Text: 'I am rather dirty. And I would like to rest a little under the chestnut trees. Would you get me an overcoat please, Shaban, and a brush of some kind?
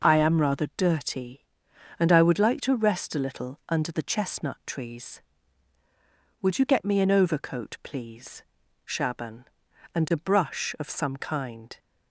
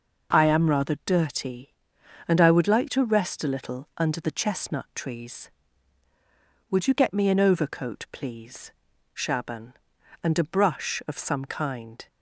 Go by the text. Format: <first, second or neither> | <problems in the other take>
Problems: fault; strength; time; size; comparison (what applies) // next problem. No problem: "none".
neither | none